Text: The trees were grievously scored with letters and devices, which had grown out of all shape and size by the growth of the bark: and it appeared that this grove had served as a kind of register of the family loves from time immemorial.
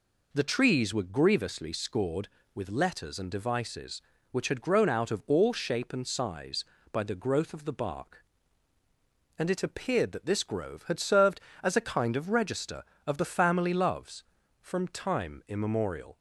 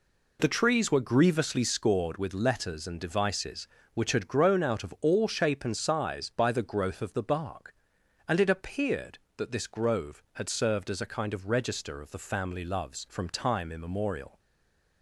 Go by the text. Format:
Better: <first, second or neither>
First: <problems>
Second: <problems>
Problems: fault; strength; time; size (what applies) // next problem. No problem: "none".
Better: first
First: none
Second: stays silent after the last word; slight; from 14.3 s on; 0.7 s long